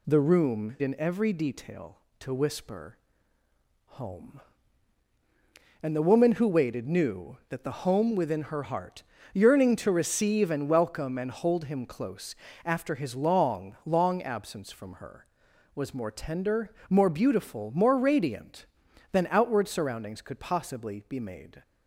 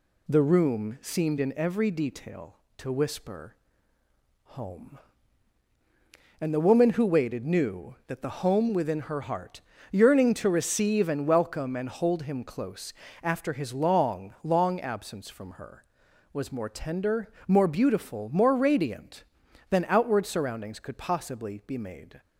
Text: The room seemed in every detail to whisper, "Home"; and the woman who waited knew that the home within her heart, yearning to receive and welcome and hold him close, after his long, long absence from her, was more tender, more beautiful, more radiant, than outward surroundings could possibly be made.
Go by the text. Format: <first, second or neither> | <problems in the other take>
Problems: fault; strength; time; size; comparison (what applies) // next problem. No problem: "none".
second | skips "seemed"; at 0.7 s